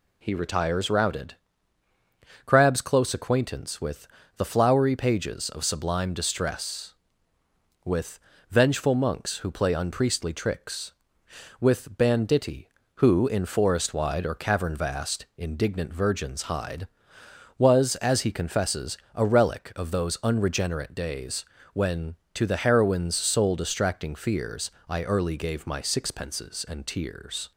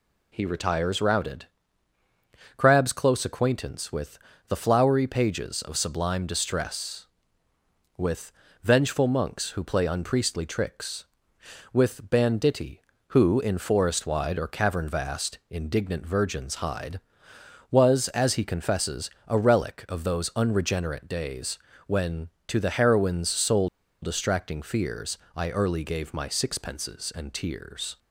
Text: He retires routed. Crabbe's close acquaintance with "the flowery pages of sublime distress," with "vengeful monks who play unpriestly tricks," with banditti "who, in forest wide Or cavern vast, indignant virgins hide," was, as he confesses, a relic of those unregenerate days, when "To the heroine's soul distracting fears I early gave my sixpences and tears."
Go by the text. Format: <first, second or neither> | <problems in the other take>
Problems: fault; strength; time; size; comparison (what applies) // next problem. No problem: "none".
first | pauses between "with" and "the"; slight; at 4.1 s; 0.30 s long; slight in the first // pauses between "with" and "vengeful"; slight; at 8.3 s; 0.32 s long; slight in the first // pauses between "soul" and "distracting"; slight; at 23.6 s; 0.33 s long // pauses between "fears" and "I"; slight; at 25.1 s; 0.20 s long; slight in the first